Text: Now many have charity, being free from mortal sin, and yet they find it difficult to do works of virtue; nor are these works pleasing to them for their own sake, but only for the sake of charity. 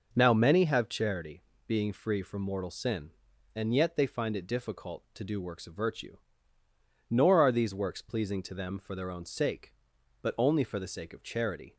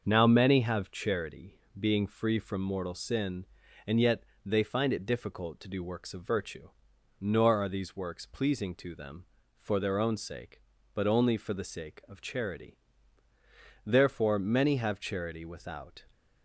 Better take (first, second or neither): first